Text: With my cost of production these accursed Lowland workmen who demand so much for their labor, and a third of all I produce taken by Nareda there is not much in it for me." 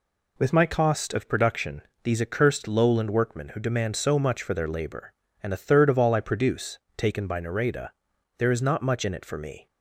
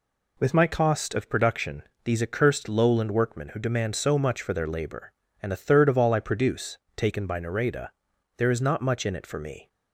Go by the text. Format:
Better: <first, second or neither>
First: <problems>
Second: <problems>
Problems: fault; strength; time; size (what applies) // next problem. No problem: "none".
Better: neither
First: pauses between "production" and "these"; slight; at 1.8 s; 0.22 s long // pauses between "produce" and "taken"; slight; at 6.7 s; 0.20 s long // pauses between "Nareda" and "there"; noticeable; at 7.8 s; 0.48 s long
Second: pauses between "production" and "these"; slight; at 1.8 s; 0.22 s long // pauses between "produce" and "taken"; slight; at 6.7 s; 0.20 s long // pauses between "Nareda" and "there"; noticeable; at 7.8 s; 0.48 s long